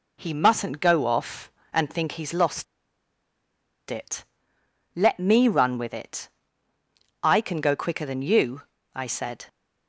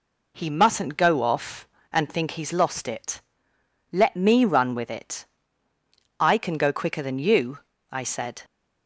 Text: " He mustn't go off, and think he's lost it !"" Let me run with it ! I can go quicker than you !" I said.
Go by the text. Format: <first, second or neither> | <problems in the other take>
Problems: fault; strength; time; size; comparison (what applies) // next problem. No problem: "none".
second | pauses between "lost" and "it"; strong; at 2.6 s; 1.2 s long